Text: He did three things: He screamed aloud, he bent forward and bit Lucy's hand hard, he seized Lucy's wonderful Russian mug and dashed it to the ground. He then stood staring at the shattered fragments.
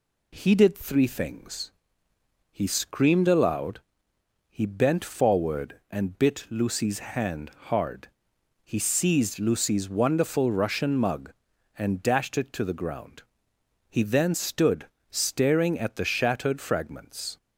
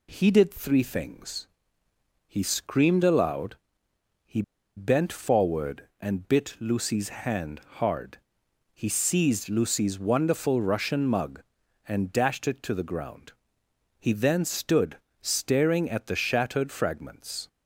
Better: first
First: pauses between "hand" and "hard"; slight; at 7.4 s; 0.18 s long // pauses between "stood" and "staring"; slight; at 14.8 s; 0.22 s long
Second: pauses between "he" and "bent"; slight; at 4.4 s; 0.35 s long // pauses between "hand" and "hard"; slight; at 7.5 s; 0.18 s long // pauses between "stood" and "staring"; slight; at 14.9 s; 0.22 s long

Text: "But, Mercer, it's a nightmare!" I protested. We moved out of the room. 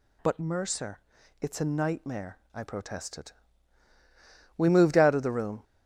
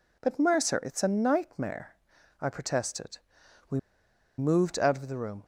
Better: first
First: none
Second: pauses between "We" and "moved"; noticeable; at 3.7 s; 0.58 s long

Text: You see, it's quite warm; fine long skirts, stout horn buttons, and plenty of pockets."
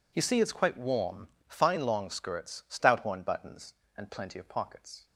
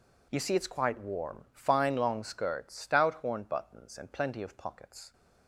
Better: neither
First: none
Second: none

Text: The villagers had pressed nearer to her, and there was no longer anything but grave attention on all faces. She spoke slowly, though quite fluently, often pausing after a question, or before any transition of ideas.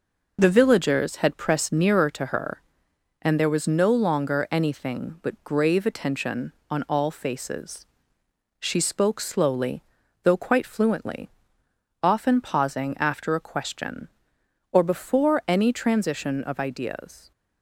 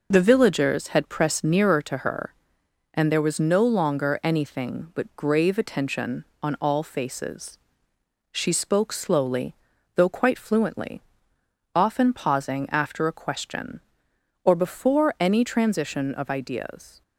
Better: neither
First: none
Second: none

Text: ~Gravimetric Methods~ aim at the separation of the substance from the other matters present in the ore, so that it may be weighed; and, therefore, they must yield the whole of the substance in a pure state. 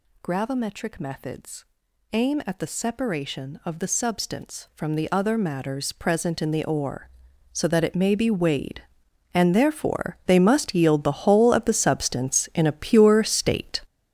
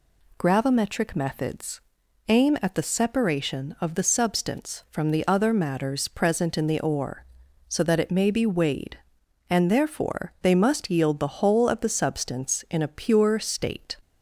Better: second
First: gets louder; strong; throughout; 9.5 dB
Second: none

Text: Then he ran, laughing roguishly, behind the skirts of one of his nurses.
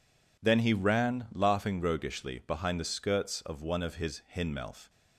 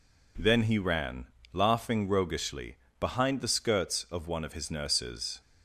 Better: second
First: says "hinmelf" for "nurses"; at 4.3 s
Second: none

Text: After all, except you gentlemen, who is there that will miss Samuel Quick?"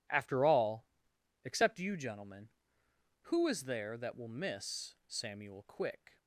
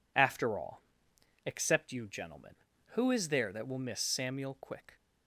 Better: neither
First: none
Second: none

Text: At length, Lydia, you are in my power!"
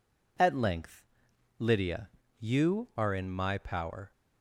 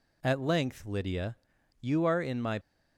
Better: first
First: none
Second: stops before "power"; at 2.6 s

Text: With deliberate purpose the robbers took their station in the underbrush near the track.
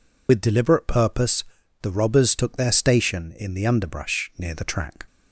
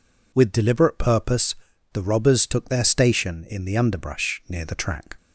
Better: second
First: loses the start of "With"; at 0.2 s; 50 ms // pauses between "purpose" and "the"; at 1.4 s; 0.40 s long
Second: pauses between "purpose" and "the"; at 1.5 s; 0.40 s long

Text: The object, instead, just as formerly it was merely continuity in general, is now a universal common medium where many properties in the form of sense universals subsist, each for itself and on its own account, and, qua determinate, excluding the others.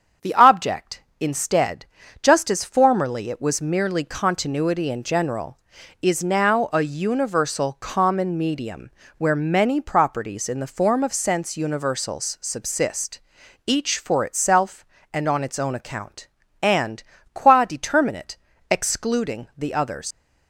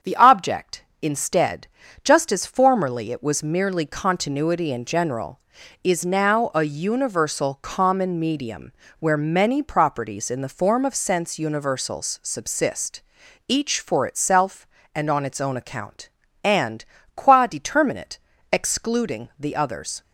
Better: second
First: starts louder than the rest; strong; until 1.3 s; 7.5 dB // pauses between "medium" and "where"; slight; at 8.9 s; 0.26 s long // leaves "others" unfinished; at 20.1 s; 100 ms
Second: starts louder than the rest; strong; until 1.2 s; 7.5 dB // pauses between "medium" and "where"; slight; at 8.7 s; 0.26 s long

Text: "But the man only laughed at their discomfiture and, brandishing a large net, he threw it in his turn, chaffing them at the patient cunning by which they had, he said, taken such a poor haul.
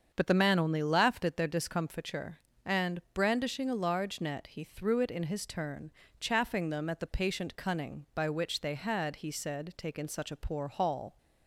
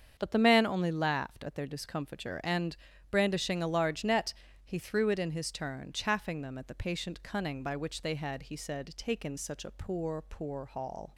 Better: first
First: starts louder than the rest; until 1.1 s; 7 dB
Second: starts louder than the rest; strong; until 1.1 s; 7.5 dB // says "poor" twice; at 10.2 s

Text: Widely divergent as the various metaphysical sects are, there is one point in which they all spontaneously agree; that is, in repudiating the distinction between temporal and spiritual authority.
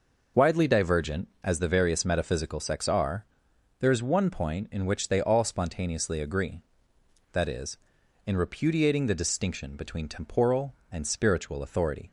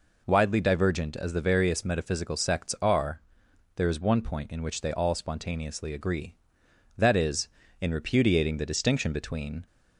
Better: first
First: none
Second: stops before "temporal and spiritual authority"; at 9.6 s

